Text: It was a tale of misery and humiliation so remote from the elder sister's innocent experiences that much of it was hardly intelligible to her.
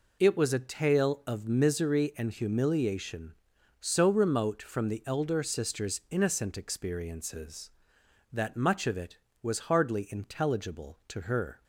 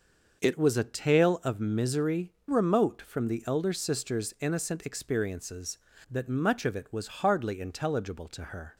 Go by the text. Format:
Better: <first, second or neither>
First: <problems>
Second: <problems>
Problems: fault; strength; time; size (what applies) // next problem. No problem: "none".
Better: first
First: none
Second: starts louder than the rest; until 1.4 s; 6 dB // skips "and humiliation so"; at 2.3 s